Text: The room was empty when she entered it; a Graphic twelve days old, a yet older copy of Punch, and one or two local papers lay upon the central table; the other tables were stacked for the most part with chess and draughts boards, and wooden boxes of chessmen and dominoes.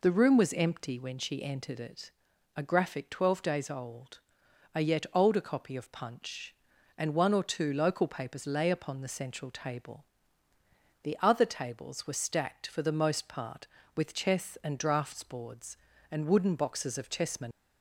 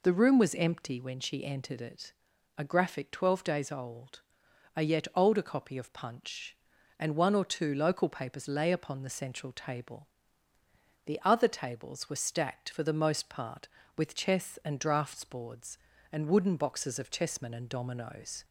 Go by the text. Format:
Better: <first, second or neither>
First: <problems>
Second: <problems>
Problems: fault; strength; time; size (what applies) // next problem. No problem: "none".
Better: second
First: stops before "and dominoes"; at 17.5 s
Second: none